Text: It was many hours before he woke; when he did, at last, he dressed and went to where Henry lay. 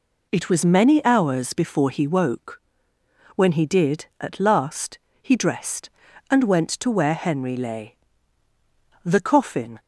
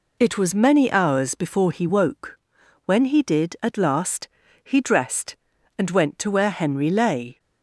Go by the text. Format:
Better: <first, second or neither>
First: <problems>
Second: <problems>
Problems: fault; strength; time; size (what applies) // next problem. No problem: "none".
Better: second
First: goes on to say "The coffin"; noticeable; from 9.0 s on; 0.76 s long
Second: none